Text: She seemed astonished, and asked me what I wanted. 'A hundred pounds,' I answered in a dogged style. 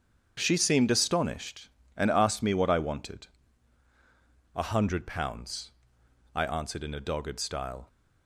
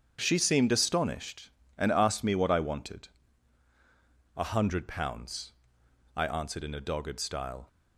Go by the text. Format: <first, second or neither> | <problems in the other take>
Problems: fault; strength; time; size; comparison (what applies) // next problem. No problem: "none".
neither | starts louder than the rest; strong; the same in both